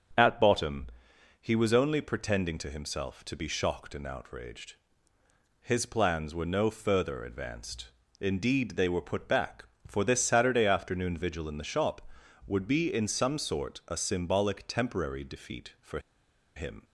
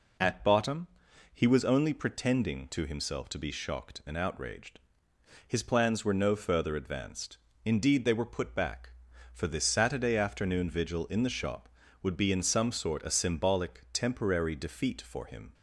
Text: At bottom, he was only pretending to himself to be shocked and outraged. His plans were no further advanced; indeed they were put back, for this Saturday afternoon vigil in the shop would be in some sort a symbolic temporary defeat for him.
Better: second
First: starts louder than the rest; until 1.7 s; 7 dB // pauses between "for" and "him"; noticeable; at 15.9 s; 0.56 s long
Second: none

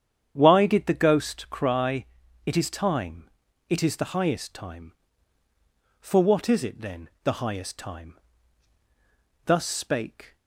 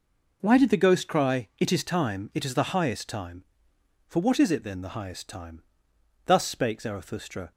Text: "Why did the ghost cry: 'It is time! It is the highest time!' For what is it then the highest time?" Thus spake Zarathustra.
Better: second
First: starts louder than the rest; strong; until 1.3 s; 8.5 dB // pauses between "then" and "the"; slight; at 7.0 s; 0.16 s long // stops before "Zarathustra"; at 10.3 s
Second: none

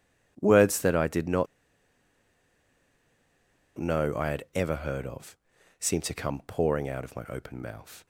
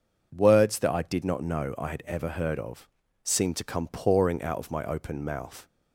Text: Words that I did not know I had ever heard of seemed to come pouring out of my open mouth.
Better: second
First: pauses between "not" and "know"; strong; at 1.4 s; 2.3 s long // pauses between "of" and "seemed"; at 5.3 s; 0.44 s long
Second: pauses between "of" and "seemed"; slight; at 2.8 s; 0.34 s long

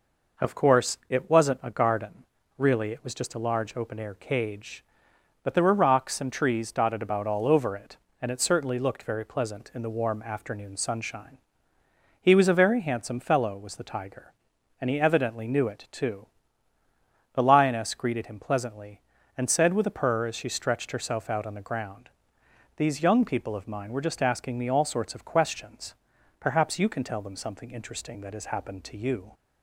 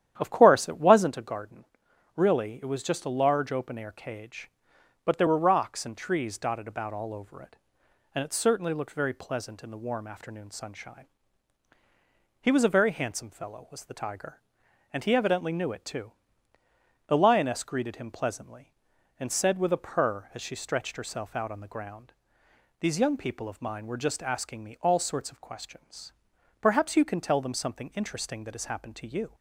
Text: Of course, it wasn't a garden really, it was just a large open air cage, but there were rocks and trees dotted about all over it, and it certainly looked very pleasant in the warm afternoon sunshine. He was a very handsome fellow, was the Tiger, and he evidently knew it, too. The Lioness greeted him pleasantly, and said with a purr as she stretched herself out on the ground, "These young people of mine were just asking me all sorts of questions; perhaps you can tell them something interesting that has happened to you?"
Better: first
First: pauses between "garden" and "really"; slight; at 2.2 s; 0.34 s long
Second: starts louder than the rest; strong; until 1.1 s; 10.5 dB // pauses between "garden" and "really"; noticeable; at 1.6 s; 0.52 s long

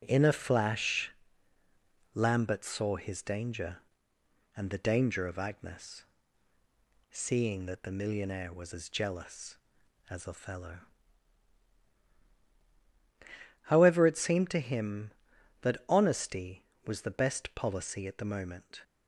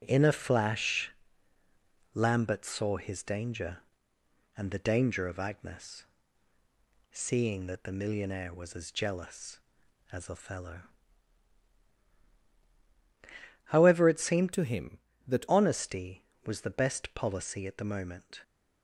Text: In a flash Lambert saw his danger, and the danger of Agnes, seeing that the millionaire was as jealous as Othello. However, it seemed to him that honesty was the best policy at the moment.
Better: first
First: pauses between "flash" and "Lambert"; at 1.1 s; 1.0 s long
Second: pauses between "flash" and "Lambert"; at 1.1 s; 1.0 s long // changes voice from "to" to "that"; from 14.5 to 15.4 s; 0.9 s long

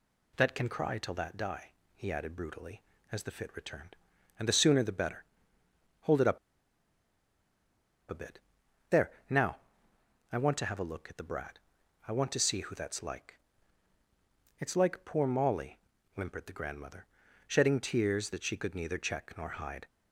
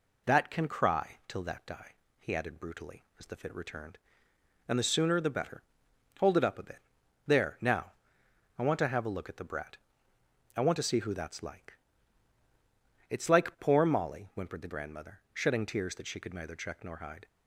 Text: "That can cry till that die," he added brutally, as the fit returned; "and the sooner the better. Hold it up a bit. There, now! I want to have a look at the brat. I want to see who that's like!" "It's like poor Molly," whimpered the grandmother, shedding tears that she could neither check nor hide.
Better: second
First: pauses between "up" and "a"; strong; at 6.3 s; 1.7 s long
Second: none

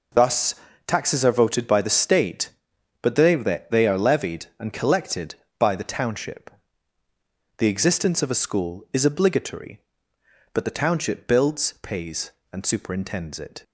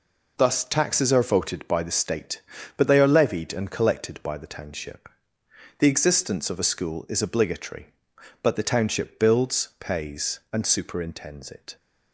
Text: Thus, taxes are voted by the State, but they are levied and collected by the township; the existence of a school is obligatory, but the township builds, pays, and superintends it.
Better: second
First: says "they" twice; at 3.7 s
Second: none

